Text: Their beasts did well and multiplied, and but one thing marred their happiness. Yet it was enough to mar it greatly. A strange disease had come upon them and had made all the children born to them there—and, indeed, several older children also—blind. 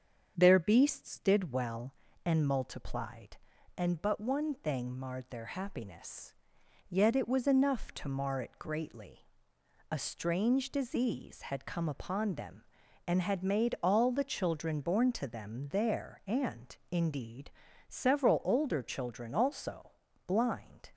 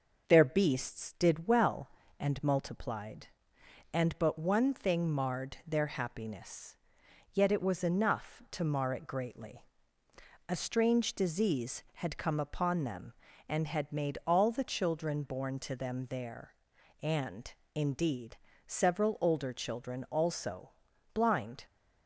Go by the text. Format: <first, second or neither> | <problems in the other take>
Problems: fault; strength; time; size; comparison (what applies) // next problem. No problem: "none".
neither | starts louder than the rest; the same in both